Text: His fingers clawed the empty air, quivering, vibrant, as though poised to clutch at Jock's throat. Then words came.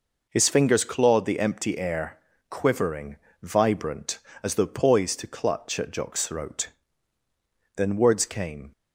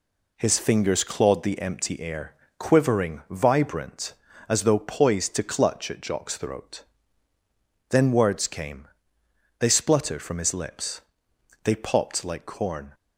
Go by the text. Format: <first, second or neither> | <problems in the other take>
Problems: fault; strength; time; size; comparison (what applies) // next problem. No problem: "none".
first | goes on to say "They spluttered from his lips They popped like corn"; strong; from 9.6 s on; 3.3 s long